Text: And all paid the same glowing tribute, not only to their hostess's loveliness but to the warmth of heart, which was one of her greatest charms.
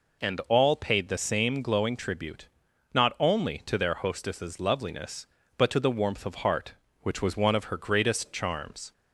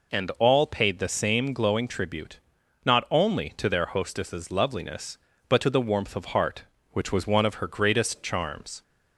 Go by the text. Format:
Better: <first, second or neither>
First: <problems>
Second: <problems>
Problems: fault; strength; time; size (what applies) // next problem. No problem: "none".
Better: neither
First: none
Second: none